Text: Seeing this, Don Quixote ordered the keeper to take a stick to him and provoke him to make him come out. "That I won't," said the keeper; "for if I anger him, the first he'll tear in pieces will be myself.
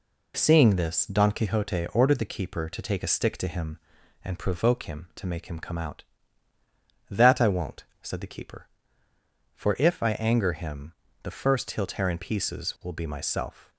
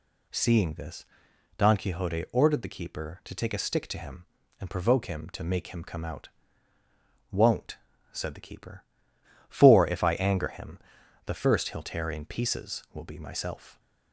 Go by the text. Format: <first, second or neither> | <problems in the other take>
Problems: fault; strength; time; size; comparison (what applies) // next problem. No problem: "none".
first | skips "That I"; at 6.7 s